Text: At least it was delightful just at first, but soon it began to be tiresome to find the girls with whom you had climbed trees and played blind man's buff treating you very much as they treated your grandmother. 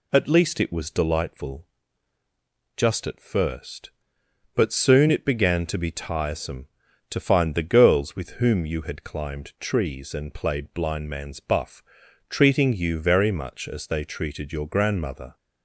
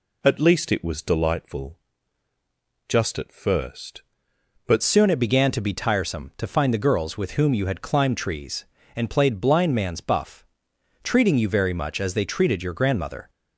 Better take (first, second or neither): first